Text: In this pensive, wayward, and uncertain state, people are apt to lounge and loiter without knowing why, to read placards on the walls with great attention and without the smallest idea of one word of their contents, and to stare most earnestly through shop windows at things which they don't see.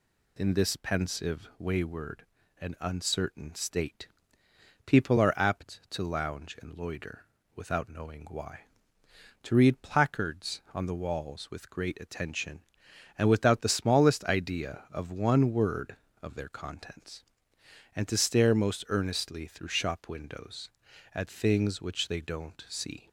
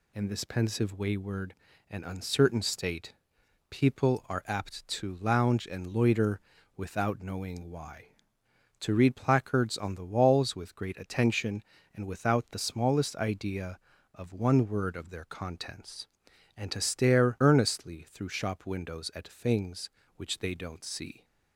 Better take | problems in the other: first | pauses between "loiter" and "without"; slight; at 6.3 s; 0.36 s long; slight in the first // skips "most"; at 17.3 s

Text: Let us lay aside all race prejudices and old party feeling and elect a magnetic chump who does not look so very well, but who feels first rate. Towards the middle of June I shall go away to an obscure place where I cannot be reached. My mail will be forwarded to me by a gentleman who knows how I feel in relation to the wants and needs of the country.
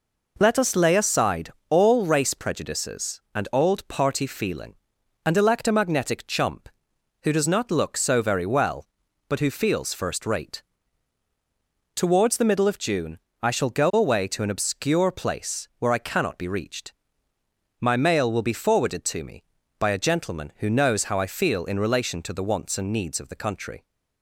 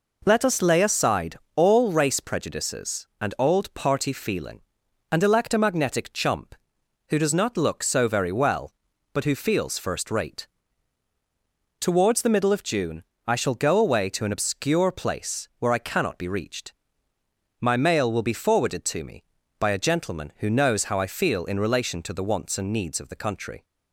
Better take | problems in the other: neither | pauses between "aside" and "all"; slight; the same in both // pauses between "June" and "I"; slight; the same in both

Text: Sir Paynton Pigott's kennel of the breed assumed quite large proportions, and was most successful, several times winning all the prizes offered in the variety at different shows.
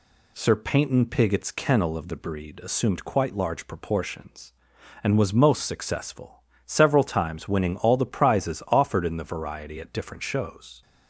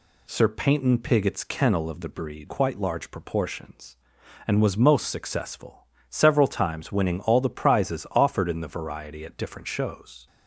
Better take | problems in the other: first | skips "assumed"; at 2.4 s

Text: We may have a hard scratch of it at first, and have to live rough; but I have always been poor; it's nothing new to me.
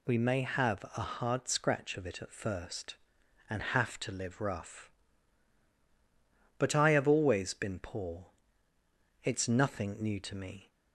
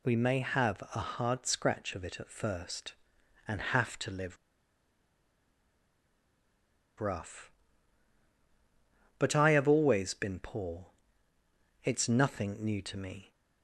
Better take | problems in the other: first | pauses between "live" and "rough"; strong; at 4.3 s; 2.6 s long

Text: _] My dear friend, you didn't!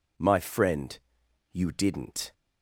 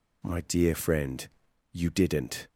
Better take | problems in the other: second | skips "dear"; at 0.3 s

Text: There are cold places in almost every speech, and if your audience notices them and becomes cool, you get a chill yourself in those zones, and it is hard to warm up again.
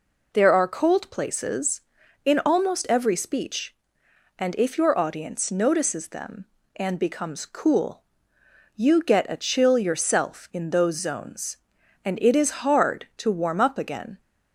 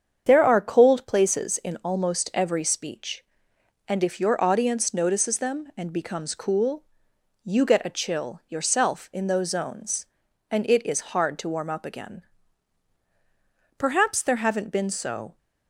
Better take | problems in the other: first | starts louder than the rest; strong; until 1.2 s; 7.5 dB // goes on to say "Perhaps there haven't been so"; from 13.7 s on; 1.6 s long

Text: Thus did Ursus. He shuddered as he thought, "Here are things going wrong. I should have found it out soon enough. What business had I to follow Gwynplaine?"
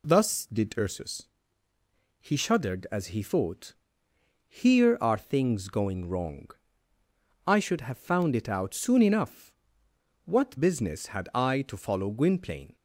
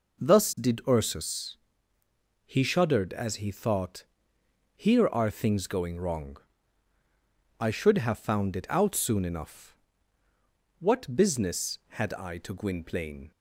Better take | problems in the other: first | skips "follow"; at 12.5 s

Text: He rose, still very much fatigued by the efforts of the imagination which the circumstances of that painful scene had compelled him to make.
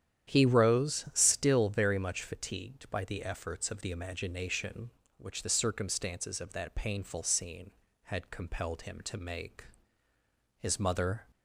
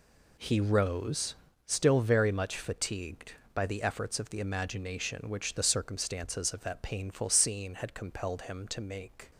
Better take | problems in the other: second | starts louder than the rest; strong; until 1.3 s; 10 dB // goes on to say "His mother"; noticeable; from 10.5 s on; 0.70 s long

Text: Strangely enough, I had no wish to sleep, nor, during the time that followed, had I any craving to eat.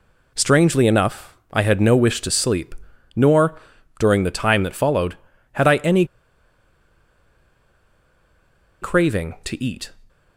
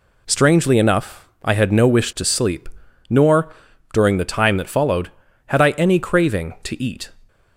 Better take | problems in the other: second | pauses between "any" and "craving"; strong; at 6.0 s; 2.7 s long

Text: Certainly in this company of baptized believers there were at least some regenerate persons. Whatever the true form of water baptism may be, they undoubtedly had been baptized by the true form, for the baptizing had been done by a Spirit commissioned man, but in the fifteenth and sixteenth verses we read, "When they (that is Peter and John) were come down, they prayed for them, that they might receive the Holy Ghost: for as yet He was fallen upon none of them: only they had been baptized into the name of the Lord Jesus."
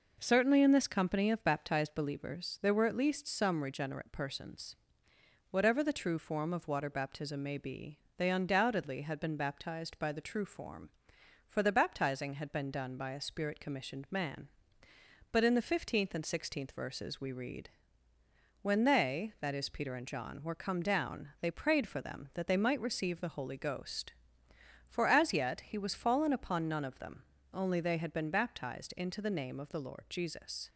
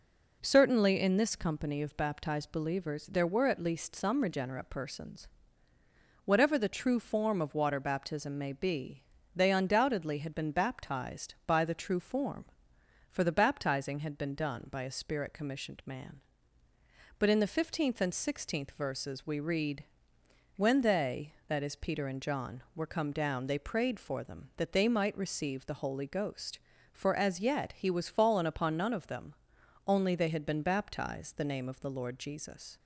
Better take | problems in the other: first | skips "into"; at 31.3 s

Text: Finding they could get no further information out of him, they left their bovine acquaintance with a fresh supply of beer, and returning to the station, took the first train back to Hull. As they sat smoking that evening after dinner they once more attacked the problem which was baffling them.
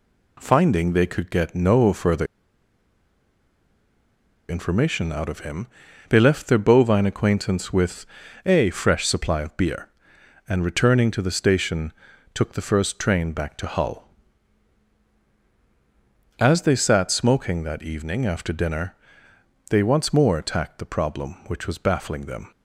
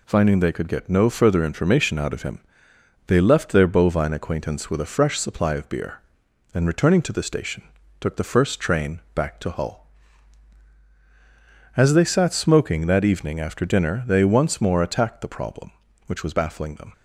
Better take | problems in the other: second | pauses between "further" and "information"; strong; at 2.2 s; 2.2 s long // pauses between "with" and "a"; at 8.0 s; 0.40 s long // pauses between "dinner" and "they"; noticeable; at 18.9 s; 0.74 s long

